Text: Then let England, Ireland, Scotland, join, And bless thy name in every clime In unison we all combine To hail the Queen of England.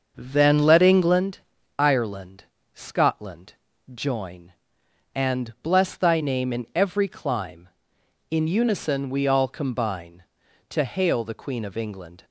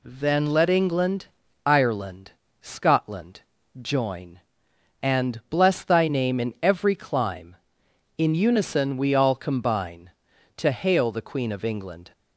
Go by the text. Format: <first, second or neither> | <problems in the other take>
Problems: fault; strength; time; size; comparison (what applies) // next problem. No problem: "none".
second | starts louder than the rest; until 1.2 s; 6.5 dB